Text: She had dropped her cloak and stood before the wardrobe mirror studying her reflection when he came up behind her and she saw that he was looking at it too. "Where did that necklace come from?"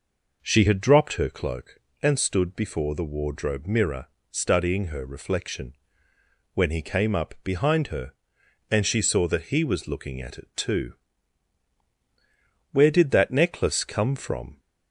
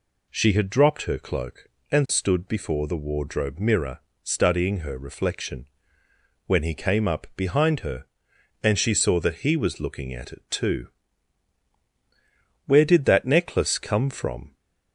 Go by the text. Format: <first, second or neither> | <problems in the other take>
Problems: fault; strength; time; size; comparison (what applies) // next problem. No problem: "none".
second | starts louder than the rest; noticeable; until 1.4 s; 5 dB // pauses between "mirror" and "studying"; slight; at 4.0 s; 0.24 s long; slight in the second // pauses between "reflection" and "when"; noticeable; at 5.7 s; 0.80 s long; noticeable in the second